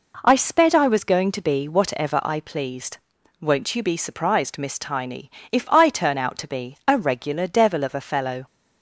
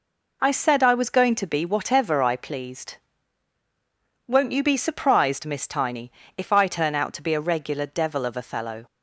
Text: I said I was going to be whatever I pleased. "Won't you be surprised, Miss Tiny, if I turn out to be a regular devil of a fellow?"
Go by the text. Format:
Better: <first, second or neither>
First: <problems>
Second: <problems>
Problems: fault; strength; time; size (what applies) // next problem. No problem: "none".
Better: second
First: says "sped" for "said"; at 0.3 s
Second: none